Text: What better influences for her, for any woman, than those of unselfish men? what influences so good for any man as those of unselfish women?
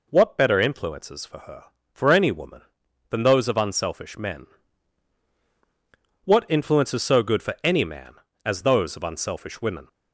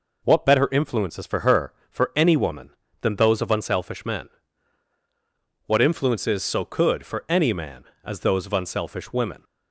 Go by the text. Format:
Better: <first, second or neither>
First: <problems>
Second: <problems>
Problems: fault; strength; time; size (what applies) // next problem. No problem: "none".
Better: first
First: none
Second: says "could" for "good"; at 6.6 s